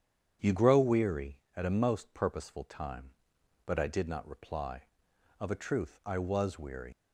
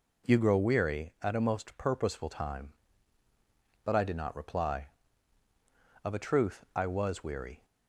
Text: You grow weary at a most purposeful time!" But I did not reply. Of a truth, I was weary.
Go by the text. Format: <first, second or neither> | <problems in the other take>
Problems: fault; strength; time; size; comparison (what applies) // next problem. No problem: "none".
second | starts louder than the rest; strong; until 1.5 s; 8.5 dB // leaves "weary" unfinished; at 6.9 s; 100 ms